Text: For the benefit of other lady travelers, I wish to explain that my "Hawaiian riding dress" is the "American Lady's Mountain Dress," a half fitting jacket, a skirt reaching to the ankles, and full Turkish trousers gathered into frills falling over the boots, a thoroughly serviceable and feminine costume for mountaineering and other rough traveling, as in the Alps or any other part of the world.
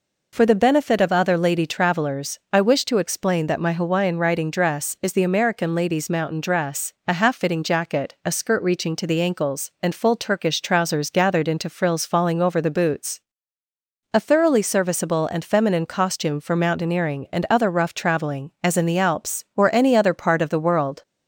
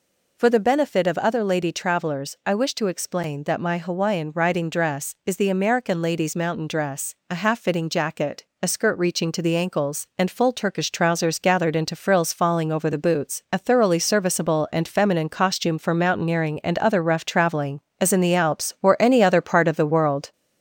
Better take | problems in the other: first | gets louder; slight; throughout; 3 dB

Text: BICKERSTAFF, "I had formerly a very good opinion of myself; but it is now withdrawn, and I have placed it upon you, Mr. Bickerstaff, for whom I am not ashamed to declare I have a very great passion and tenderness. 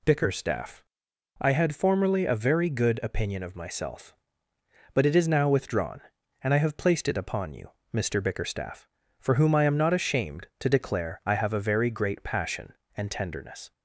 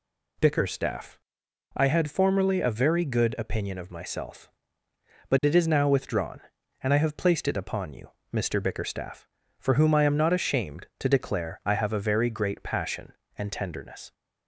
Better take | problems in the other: neither | none

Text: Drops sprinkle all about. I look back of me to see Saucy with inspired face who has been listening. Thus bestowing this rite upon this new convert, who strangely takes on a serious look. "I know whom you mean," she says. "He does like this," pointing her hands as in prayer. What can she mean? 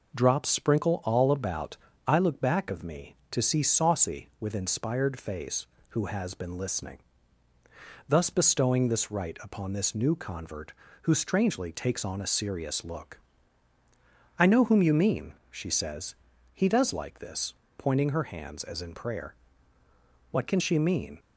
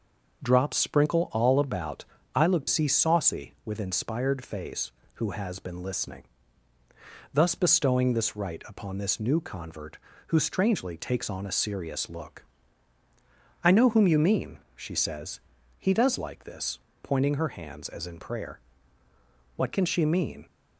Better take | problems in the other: first | starts louder than the rest; noticeable; until 1.4 s; 6 dB // skips "back of me to"; at 2.6 s

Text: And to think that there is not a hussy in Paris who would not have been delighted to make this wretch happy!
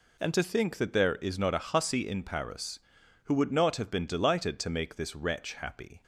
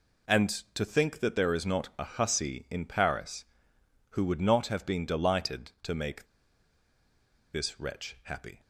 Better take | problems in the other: first | pauses between "make" and "this"; strong; at 6.2 s; 1.2 s long

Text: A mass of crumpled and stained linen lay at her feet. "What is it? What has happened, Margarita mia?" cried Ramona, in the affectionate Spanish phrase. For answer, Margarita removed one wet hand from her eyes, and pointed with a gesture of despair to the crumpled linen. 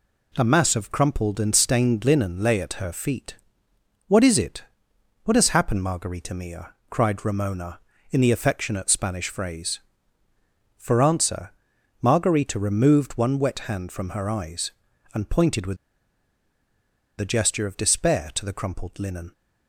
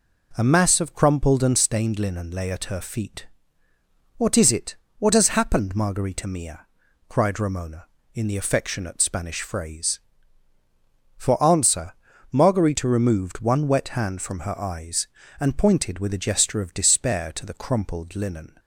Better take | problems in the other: second | pauses between "with" and "a"; strong; at 15.7 s; 1.4 s long

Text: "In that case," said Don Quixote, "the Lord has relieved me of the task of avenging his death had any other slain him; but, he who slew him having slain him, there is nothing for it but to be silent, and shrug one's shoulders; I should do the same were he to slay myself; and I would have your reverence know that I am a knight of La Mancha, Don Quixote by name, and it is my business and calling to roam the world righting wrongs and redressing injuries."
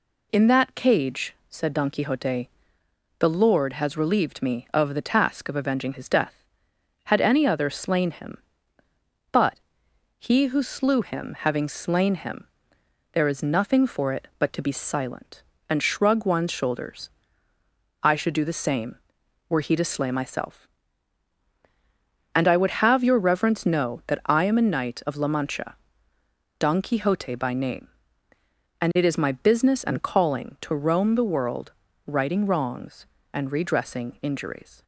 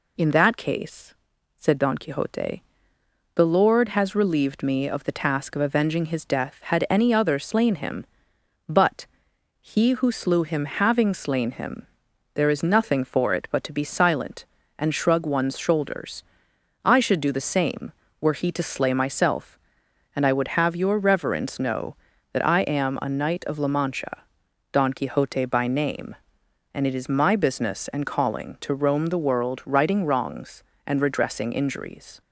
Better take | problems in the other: second | says "cage" for "case"; at 0.7 s // pauses between "world" and "righting"; slight; at 31.7 s; 0.34 s long

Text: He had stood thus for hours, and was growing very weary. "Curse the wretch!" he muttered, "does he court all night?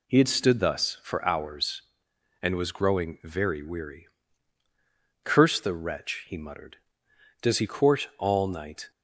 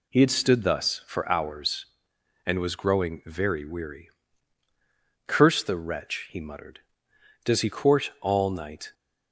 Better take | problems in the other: neither | none

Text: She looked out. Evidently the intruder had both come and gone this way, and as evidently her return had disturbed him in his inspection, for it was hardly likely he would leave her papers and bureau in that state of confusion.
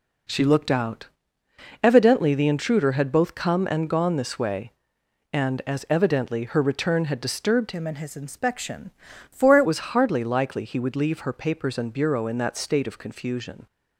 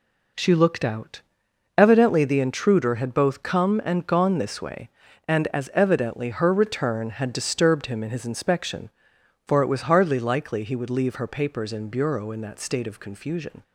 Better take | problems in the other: second | changes voice from "him" to "it"; from 7.7 to 9.6 s; 1.9 s long

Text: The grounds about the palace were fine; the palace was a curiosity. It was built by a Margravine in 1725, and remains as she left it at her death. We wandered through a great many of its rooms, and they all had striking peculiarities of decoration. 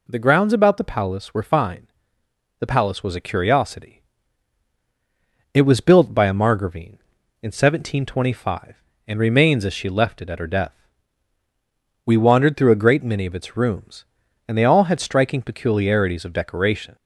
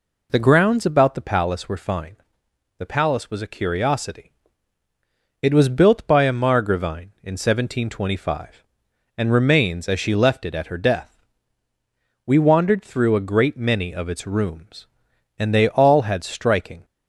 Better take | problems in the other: first | stops before "peculiarities of decoration"; at 16.8 s

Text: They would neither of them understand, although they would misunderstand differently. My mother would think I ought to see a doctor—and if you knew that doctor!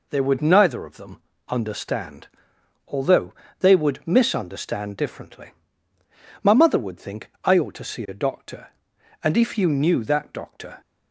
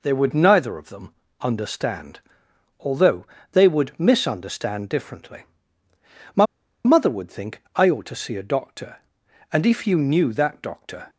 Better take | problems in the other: first | pauses between "them" and "understand"; slight; at 1.1 s; 0.28 s long; slight in the first // pauses between "although" and "they"; slight; at 3.2 s; 0.26 s long; slight in the first // pauses between "My" and "mother"; at 6.4 s; 0.39 s long

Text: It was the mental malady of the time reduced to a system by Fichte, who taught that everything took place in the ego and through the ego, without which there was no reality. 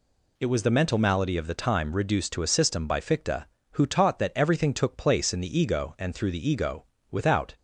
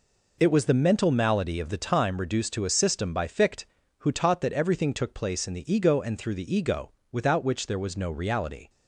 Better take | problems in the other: second | stops before "which there was no reality"; at 7.5 s

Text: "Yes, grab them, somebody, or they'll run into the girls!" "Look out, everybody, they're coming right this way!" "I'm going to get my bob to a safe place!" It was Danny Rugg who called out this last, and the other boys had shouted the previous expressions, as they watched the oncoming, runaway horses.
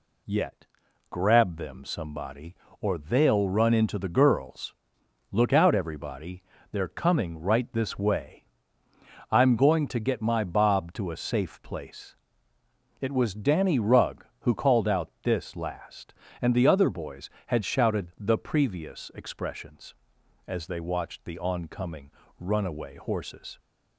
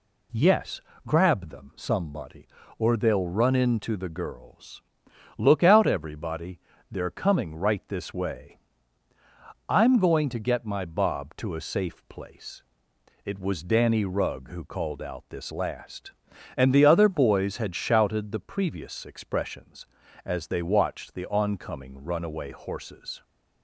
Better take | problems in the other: second | says "Yet" for "Yes"; at 0.2 s

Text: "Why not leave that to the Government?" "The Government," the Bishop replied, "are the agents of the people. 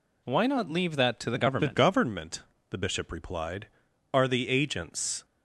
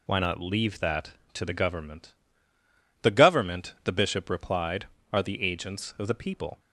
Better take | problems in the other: second | stops before "of the people"; at 5.2 s

